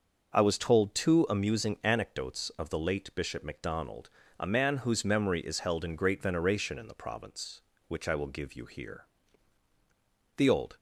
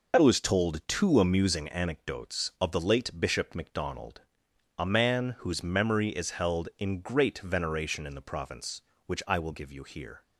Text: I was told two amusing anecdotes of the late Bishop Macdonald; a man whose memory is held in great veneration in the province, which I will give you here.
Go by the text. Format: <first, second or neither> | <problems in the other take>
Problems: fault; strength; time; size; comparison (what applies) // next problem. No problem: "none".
second | starts louder than the rest; until 1.3 s; 6.5 dB // goes on to say "The old"; slight; from 10.3 s on; 0.42 s long